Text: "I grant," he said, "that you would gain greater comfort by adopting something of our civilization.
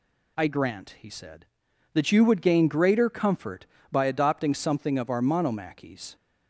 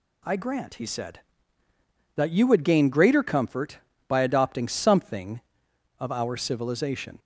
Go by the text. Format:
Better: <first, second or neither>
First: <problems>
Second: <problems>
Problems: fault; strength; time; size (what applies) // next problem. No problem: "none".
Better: second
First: says "monomachies" for "civilization"; at 5.2 s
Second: none